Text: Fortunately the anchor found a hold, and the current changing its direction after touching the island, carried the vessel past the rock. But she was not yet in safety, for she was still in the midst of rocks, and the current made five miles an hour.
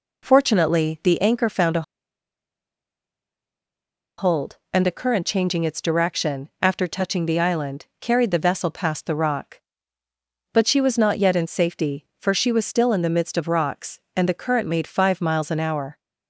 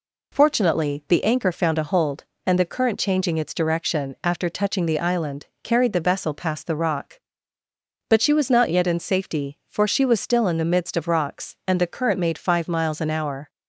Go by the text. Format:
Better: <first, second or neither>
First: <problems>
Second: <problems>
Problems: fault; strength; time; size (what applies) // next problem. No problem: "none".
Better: second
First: pauses between "a" and "hold"; strong; at 1.8 s; 2.3 s long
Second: none